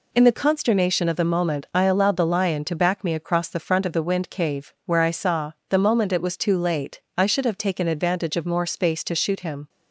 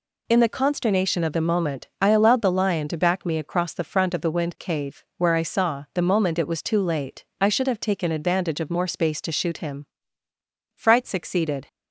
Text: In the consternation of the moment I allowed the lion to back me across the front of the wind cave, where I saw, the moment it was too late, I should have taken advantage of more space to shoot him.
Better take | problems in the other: first | goes on to say "Fright succeeded"; noticeable; from 10.7 s on; 0.92 s long

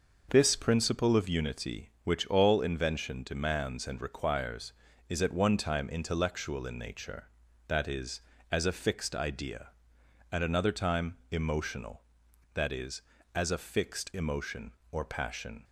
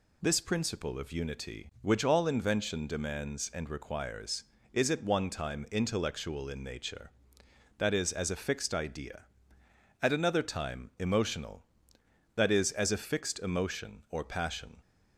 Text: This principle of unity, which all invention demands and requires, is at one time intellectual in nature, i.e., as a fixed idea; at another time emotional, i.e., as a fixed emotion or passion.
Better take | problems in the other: neither | none

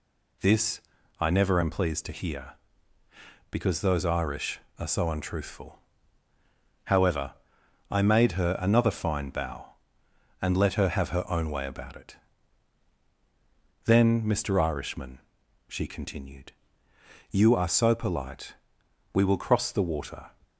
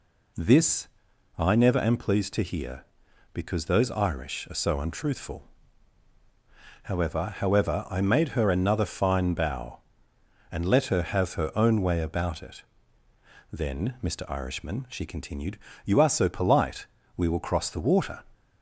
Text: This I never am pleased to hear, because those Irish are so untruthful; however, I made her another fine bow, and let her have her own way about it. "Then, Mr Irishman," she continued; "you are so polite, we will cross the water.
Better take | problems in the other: first | pauses between "This" and "I"; noticeable; at 0.8 s; 0.50 s long; slight in the first // says "however" twice; at 7.3 s

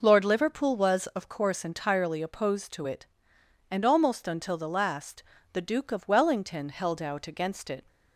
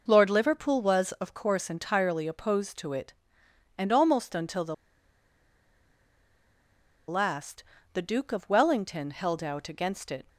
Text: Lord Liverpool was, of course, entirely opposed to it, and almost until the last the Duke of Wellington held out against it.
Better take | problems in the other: first | pauses between "the" and "last"; strong; at 4.7 s; 2.3 s long // pauses between "last" and "the"; slight; at 7.6 s; 0.30 s long; slight in the first

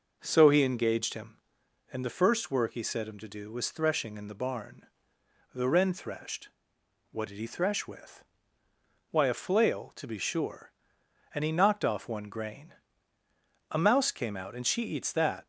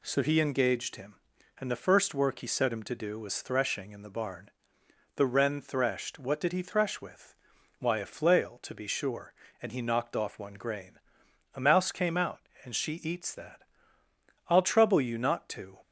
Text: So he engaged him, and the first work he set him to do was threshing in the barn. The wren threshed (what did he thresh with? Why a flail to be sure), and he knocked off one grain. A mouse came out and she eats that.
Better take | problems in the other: first | goes on to say "I'll trouble you not to"; noticeable; from 14.4 s on; 1.3 s long

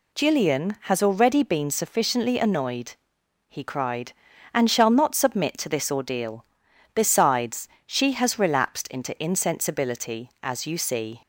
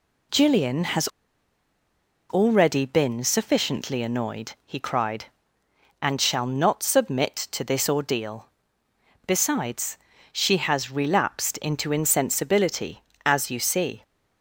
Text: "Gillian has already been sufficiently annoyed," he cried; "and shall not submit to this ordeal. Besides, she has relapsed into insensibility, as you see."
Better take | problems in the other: first | pauses between "has" and "already"; at 1.0 s; 1.2 s long

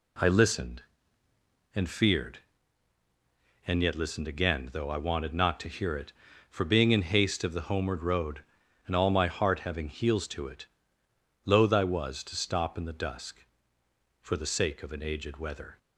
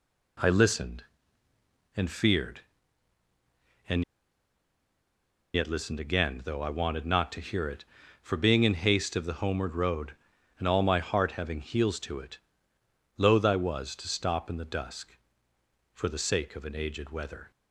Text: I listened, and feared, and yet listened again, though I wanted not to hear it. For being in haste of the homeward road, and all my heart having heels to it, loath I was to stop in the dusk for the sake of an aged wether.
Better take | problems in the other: first | pauses between "and" and "yet"; strong; at 4.0 s; 1.5 s long

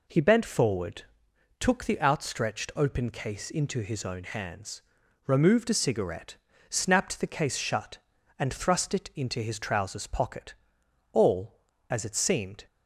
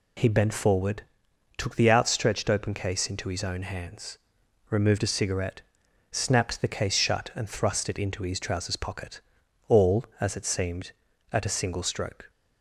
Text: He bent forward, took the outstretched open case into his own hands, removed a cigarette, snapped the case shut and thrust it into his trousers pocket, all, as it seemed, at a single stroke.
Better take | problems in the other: second | stops before "at a single stroke"; at 12.6 s

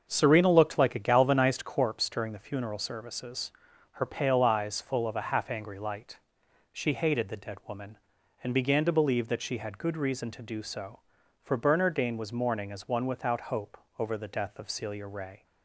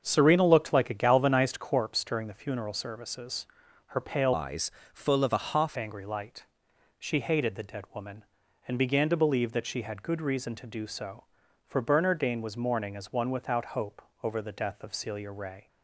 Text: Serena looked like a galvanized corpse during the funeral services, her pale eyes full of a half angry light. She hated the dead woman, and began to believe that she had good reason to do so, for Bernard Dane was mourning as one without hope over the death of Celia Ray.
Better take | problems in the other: first | starts louder than the rest; until 1.0 s; 6.5 dB; also in the first // changes voice from "eyes" to "half"; from 4.3 to 5.7 s; 1.4 s long // pauses between "eyes" and "full"; slight; at 4.7 s; 0.24 s long // pauses between "hope" and "over"; slight; at 14.0 s; 0.22 s long; slight in the first

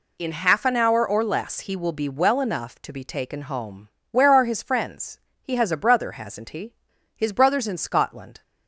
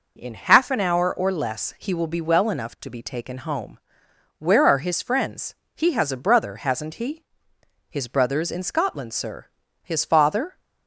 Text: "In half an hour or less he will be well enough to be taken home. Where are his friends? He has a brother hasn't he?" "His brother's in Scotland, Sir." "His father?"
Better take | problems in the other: second | stops before "Sir His father"; at 8.4 s

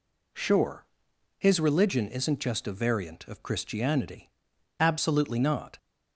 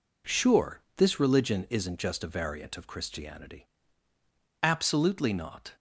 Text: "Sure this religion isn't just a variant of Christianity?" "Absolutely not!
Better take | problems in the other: second | says "his" for "this"; at 1.3 s

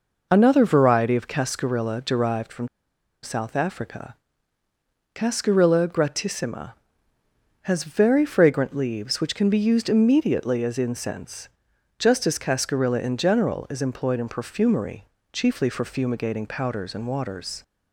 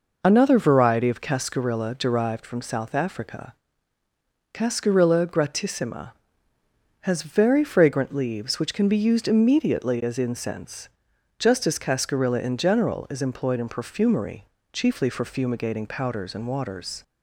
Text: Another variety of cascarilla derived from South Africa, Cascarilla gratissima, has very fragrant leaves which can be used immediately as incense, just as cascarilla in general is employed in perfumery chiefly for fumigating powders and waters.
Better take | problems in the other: second | pauses between "from" and "South"; noticeable; at 2.6 s; 0.54 s long // pauses between "perfumery" and "chiefly"; slight; at 15.0 s; 0.26 s long; slight in the second

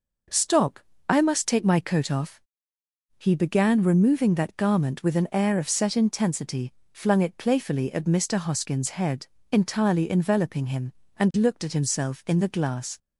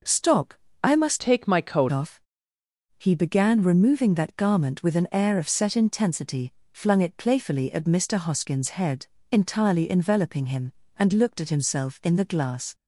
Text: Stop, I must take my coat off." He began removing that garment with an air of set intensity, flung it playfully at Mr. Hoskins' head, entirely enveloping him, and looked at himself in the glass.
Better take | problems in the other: first | changes voice from "take" to "coat"; from 1.1 to 1.9 s; 0.8 s long

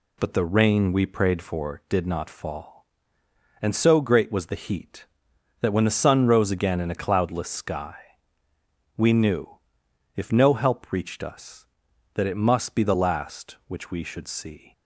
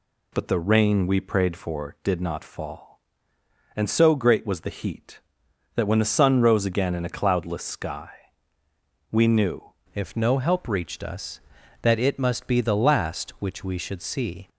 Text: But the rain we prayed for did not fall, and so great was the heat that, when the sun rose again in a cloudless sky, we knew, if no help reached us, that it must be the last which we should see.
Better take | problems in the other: first | changes voice at "if"; from 9.9 s on; 4.5 s long

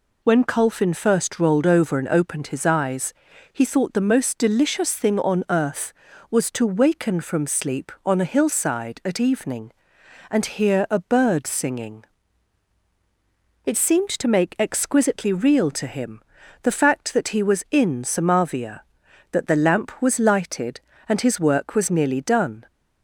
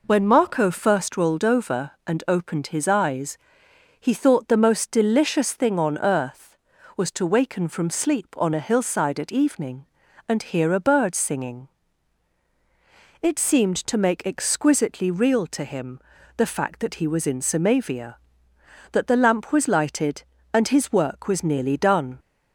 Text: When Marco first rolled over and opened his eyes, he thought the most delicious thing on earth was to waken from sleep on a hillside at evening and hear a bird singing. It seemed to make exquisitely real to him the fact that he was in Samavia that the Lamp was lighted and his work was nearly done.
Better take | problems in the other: second | says "Colfin" for "Marco"; at 0.4 s // pauses between "him" and "the"; at 16.2 s; 0.42 s long; also in the second

